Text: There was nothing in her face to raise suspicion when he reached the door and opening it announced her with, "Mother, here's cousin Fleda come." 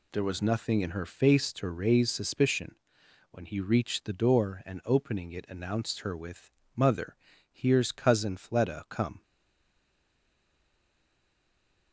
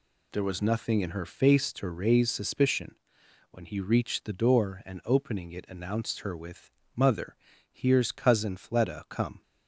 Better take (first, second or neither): second